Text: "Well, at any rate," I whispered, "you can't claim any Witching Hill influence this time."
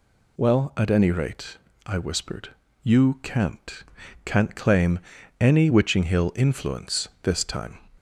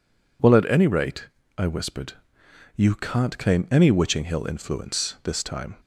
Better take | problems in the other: second | says "can't" twice; at 4.2 s // pauses between "claim" and "any"; at 4.9 s; 0.40 s long

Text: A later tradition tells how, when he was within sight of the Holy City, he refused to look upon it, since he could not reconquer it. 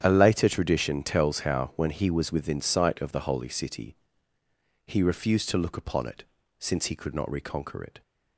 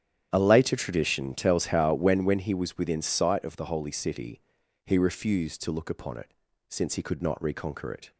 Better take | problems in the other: first | starts louder than the rest; strong; until 1.3 s; 10 dB; strong in the first // says "when" twice; at 2.2 s

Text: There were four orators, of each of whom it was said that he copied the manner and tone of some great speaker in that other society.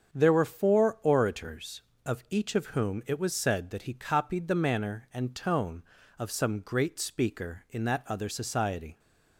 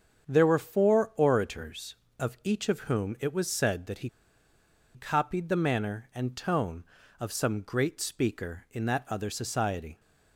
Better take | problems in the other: first | starts louder than the rest; strong; until 1.3 s; 7 dB; strong in the first // pauses between "he" and "copied"; noticeable; at 4.0 s; 0.86 s long

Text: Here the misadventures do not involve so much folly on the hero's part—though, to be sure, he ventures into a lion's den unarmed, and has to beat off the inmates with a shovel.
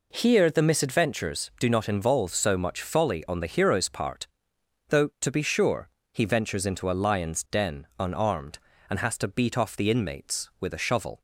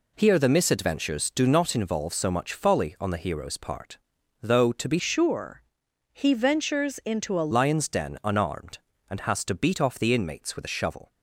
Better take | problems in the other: first | changes voice from "sure" to "a"; from 4.9 to 7.4 s; 2.5 s long

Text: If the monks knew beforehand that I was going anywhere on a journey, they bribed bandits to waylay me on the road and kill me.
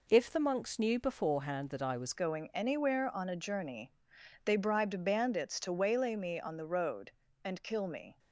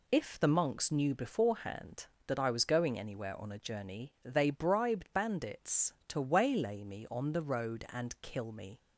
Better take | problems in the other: second | changes voice at "going"; from 2.1 s on; 6.0 s long

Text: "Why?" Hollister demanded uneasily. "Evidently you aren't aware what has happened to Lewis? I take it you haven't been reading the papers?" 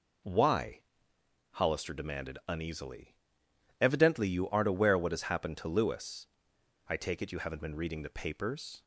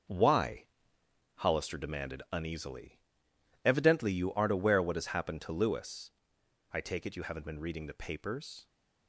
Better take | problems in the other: first | gets quieter; strong; throughout; 8 dB

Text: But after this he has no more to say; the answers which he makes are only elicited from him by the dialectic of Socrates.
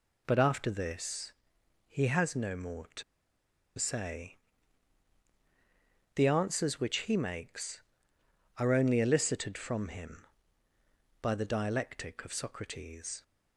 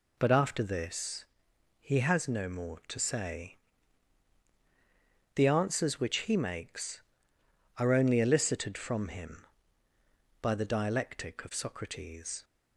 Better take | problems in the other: second | pauses between "this" and "he"; noticeable; at 1.3 s; 0.56 s long; noticeable in the second // pauses between "to" and "say"; noticeable; at 3.0 s; 0.75 s long

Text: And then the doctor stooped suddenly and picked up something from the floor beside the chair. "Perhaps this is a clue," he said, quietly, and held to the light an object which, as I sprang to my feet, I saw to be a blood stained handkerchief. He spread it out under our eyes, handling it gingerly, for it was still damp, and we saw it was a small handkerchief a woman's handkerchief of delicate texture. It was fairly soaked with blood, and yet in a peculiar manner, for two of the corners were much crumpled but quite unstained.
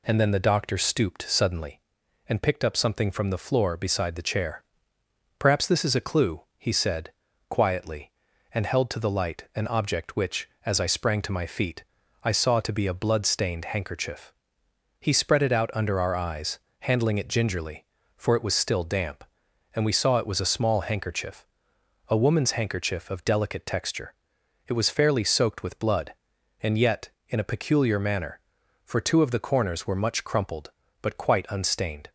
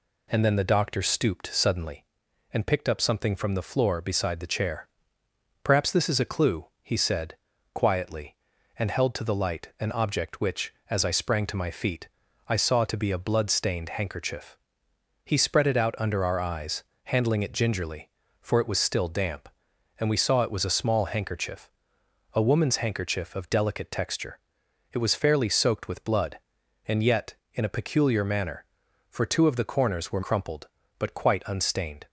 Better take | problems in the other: first | pauses between "handkerchief" and "a"; noticeable; at 21.7 s; 0.62 s long; noticeable in the first // skips "much"; at 30.2 s

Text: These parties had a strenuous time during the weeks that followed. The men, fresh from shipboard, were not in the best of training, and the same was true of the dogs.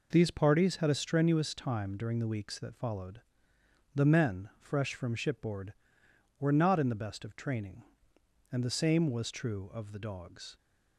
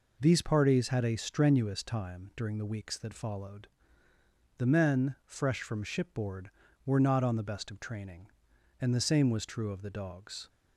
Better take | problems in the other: first | says "on" for "in"; at 7.2 s

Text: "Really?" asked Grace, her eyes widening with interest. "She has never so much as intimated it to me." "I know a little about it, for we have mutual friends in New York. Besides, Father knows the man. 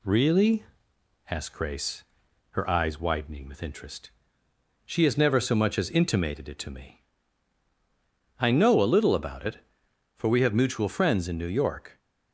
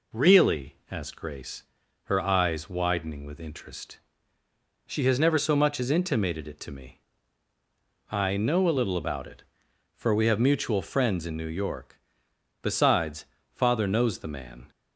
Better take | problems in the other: second | stops before "Besides Father knows the man"; at 11.9 s

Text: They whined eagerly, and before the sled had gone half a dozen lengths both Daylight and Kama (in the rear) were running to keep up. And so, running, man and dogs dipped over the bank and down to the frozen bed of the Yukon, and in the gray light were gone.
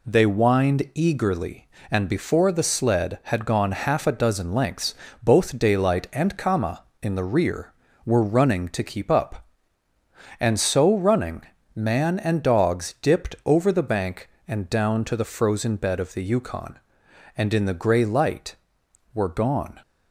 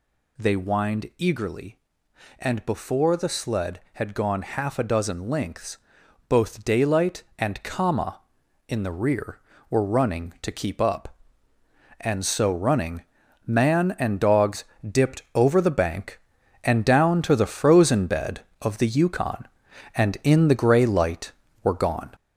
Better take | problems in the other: first | gets louder; noticeable; throughout; 5.5 dB // pauses between "lengths" and "both"; noticeable; at 5.7 s; 0.50 s long; slight in the first // pauses between "dogs" and "dipped"; slight; at 14.6 s; 0.26 s long

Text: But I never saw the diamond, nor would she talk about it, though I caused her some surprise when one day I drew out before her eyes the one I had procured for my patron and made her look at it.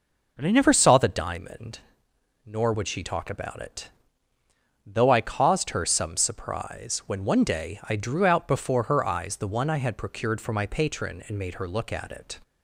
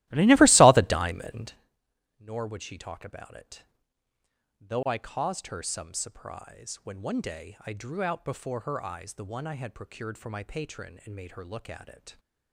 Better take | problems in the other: first | starts louder than the rest; strong; until 1.7 s; 16.5 dB

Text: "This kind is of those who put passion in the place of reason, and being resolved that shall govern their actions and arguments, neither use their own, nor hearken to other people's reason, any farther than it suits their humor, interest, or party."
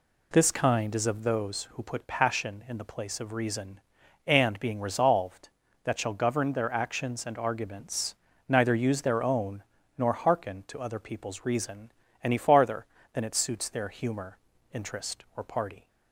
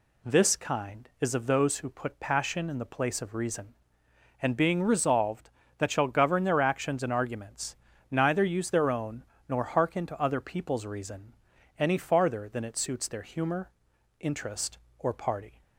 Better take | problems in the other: neither | none

